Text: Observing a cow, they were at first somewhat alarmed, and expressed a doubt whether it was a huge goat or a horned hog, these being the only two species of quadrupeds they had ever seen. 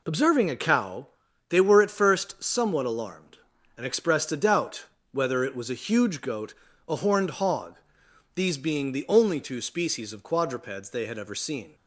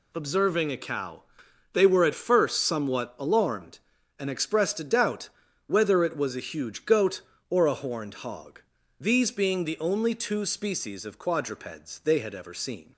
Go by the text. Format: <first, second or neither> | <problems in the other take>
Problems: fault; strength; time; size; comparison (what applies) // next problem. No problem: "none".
second | pauses between "doubt" and "whether"; slight; at 4.8 s; 0.28 s long; also in the second // skips "or"; at 6.7 s